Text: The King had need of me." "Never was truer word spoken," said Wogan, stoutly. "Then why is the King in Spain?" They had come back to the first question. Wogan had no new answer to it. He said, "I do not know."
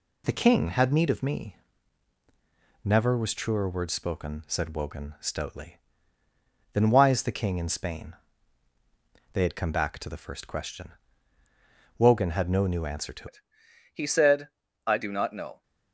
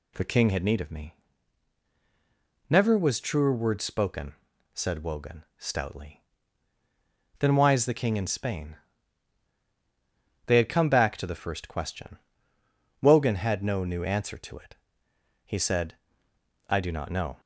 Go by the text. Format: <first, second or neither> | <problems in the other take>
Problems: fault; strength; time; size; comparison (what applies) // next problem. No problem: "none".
second | changes voice at "it"; from 13.2 s on; 2.4 s long